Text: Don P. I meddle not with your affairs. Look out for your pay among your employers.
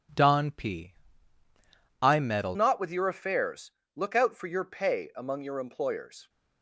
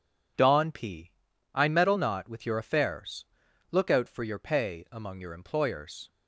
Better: second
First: changes voice at "not"; from 2.5 s on; 3.7 s long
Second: none

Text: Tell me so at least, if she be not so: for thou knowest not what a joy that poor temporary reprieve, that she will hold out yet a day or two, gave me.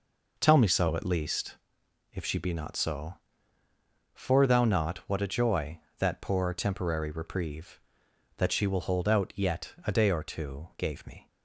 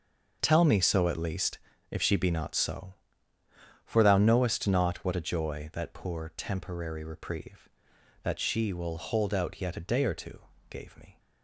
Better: second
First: skips "knowest"; at 4.6 s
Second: none

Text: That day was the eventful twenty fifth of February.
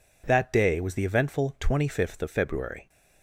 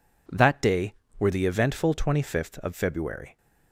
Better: first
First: none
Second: says "were" for "was"; at 1.1 s

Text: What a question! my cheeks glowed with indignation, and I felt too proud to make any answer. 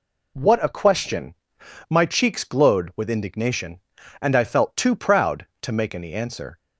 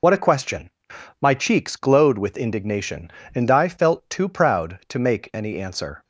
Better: first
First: none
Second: loses the start of "What"; at 0.0 s; 55 ms

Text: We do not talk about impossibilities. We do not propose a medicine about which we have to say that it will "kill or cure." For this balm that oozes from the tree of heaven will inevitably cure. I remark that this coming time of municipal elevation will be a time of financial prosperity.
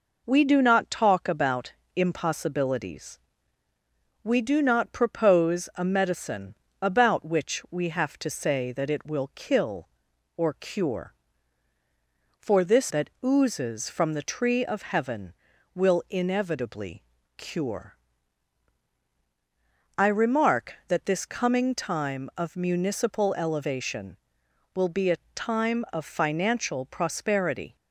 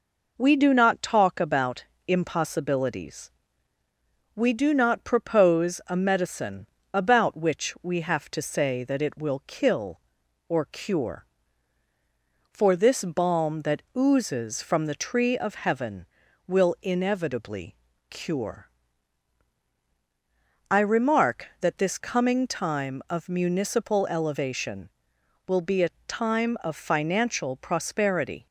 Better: second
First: pauses between "about" and "impossibilities"; slight; at 1.7 s; 0.24 s long // pauses between "medicine" and "about"; slight; at 6.5 s; 0.26 s long // skips "balm"; at 12.9 s // pauses between "inevitably" and "cure"; slight; at 17.0 s; 0.34 s long // pauses between "a" and "time"; slight; at 25.1 s; 0.18 s long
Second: pauses between "about" and "impossibilities"; slight; at 1.8 s; 0.24 s long // pauses between "medicine" and "about"; slight; at 6.6 s; 0.26 s long // pauses between "inevitably" and "cure"; slight; at 17.7 s; 0.34 s long // pauses between "a" and "time"; slight; at 25.8 s; 0.18 s long

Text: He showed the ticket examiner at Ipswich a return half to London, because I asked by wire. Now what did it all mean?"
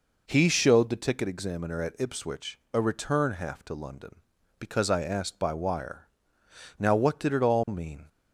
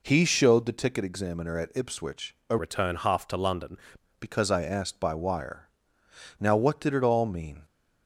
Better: first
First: pauses between "Ipswich" and "a"; slight; at 2.5 s; 0.16 s long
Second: pauses between "Ipswich" and "a"; slight; at 2.3 s; 0.16 s long // changes voice from "return" to "London"; from 2.5 to 3.7 s; 1.2 s long

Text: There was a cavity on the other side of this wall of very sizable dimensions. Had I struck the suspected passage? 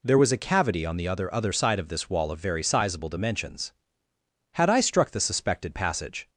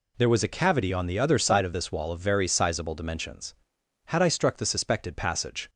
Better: second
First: says "other" twice; at 1.3 s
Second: none

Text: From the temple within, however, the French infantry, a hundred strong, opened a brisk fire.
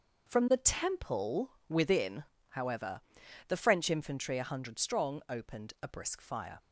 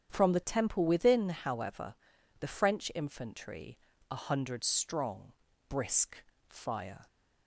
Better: first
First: none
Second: starts louder than the rest; strong; until 1.1 s; 8.5 dB // skips "opened a"; at 5.5 s // pauses between "brisk" and "fire"; slight; at 6.2 s; 0.28 s long

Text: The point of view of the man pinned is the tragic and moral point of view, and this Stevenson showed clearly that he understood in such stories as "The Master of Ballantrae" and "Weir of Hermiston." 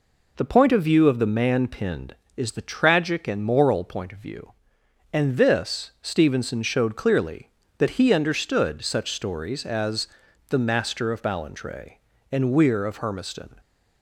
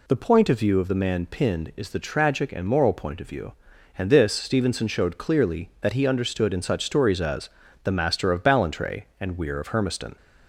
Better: second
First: skips "in"; at 8.8 s // pauses between "as" and "The"; at 10.0 s; 0.40 s long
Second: pauses between "as" and "The"; slight; at 7.4 s; 0.36 s long

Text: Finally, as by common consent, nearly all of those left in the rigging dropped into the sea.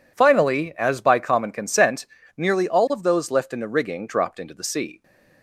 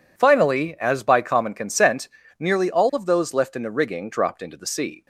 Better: neither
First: none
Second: none

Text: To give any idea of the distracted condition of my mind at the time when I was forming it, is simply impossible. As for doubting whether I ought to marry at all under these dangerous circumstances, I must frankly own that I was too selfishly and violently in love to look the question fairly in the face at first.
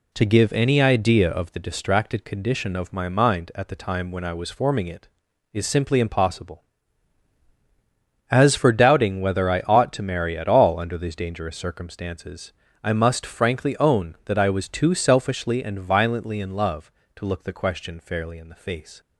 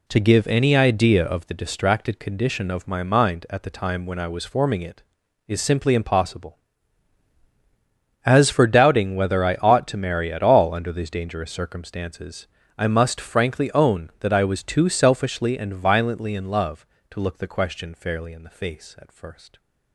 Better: second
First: stops before "at first"; at 19.0 s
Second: none

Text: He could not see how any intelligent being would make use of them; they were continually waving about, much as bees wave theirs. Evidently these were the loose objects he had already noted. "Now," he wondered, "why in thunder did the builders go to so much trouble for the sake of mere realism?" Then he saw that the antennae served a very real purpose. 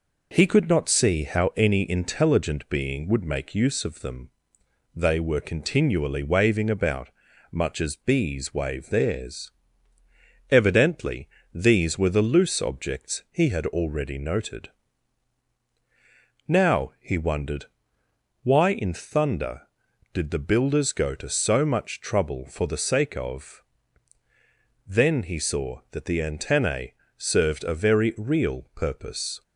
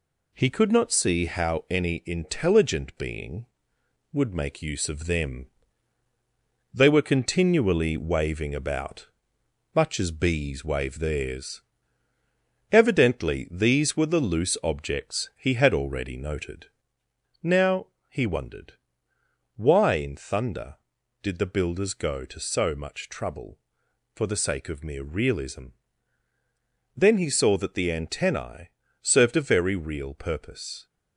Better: second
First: pauses between "Evidently" and "these"; slight; at 11.2 s; 0.26 s long // skips "mere realism"; at 24.2 s // pauses between "antennae" and "served"; slight; at 26.9 s; 0.24 s long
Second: pauses between "antennae" and "served"; slight; at 28.6 s; 0.32 s long

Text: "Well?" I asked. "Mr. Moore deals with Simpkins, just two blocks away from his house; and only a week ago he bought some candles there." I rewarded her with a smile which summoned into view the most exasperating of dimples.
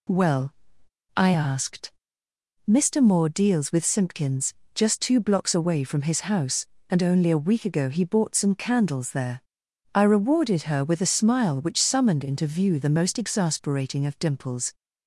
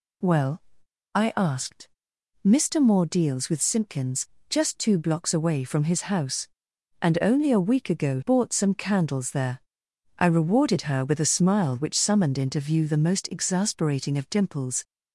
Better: first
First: none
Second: skips "he"; at 8.2 s

